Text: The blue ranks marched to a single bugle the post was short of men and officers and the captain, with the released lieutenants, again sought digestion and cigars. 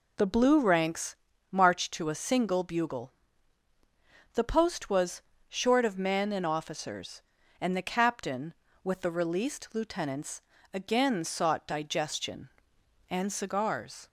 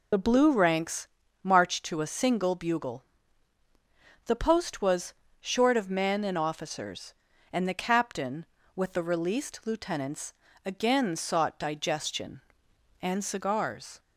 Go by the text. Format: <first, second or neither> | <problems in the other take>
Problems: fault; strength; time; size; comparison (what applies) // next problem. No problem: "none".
first | loses the start of "The"; at 0.1 s; 30 ms // pauses between "ranks" and "marched"; at 1.0 s; 0.38 s long; also in the first // pauses between "bugle" and "the"; at 3.0 s; 1.2 s long; also in the first // pauses between "was" and "short"; slight; at 5.1 s; 0.30 s long; slight in the first